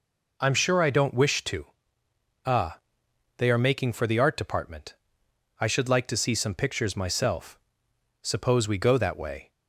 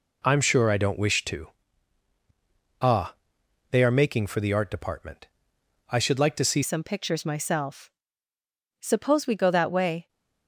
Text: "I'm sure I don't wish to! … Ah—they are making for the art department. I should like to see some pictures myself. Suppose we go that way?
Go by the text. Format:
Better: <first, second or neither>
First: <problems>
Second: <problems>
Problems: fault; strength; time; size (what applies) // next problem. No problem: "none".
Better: first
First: none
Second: changes voice at "some"; from 6.6 s on; 3.4 s long